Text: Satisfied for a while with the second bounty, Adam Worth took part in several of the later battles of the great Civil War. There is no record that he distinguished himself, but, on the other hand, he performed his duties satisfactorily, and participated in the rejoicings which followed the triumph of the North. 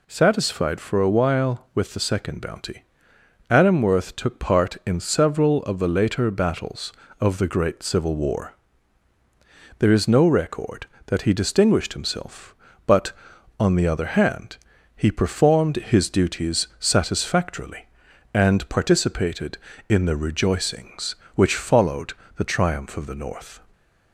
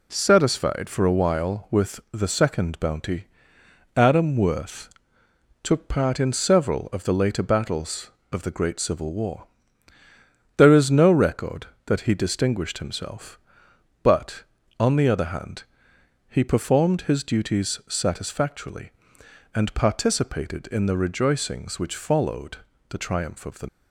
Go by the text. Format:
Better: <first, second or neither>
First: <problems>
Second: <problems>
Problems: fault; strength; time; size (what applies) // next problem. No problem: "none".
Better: first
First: pauses between "followed" and "the"; slight; at 22.1 s; 0.24 s long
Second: pauses between "Worth" and "took"; noticeable; at 4.8 s; 0.74 s long // pauses between "followed" and "the"; slight; at 22.5 s; 0.32 s long // stops before "North"; at 23.6 s